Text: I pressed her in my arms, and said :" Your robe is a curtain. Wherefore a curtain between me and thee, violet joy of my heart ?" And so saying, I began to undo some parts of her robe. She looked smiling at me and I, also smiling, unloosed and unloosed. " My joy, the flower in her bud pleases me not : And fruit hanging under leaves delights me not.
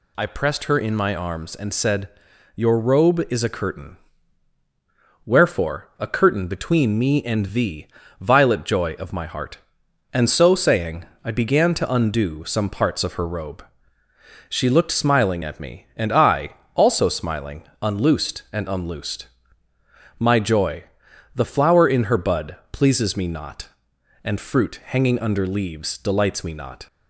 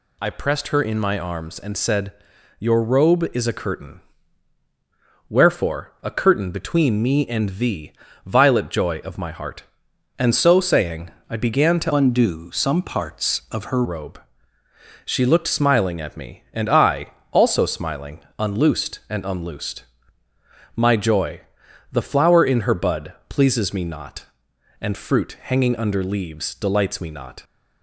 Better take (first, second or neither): first